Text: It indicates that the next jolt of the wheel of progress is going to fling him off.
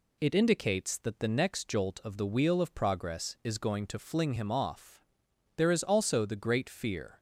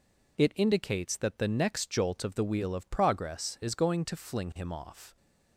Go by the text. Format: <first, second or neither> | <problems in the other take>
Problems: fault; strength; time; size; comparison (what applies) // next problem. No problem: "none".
second | goes on to say "There is also the great fear"; from 5.5 s on; 1.6 s long